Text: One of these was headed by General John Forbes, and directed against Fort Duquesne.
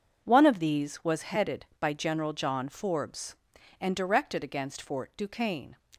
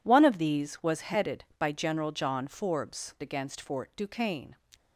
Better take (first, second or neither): first